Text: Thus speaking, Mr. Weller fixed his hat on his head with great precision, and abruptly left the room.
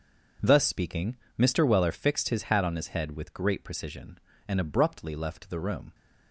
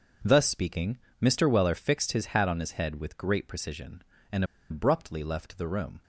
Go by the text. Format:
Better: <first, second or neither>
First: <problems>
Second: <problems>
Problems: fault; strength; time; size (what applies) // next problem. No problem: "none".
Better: first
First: starts louder than the rest; until 1.6 s; 6.5 dB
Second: starts louder than the rest; until 1.4 s; 6.5 dB // pauses between "and" and "abruptly"; slight; at 4.4 s; 0.25 s long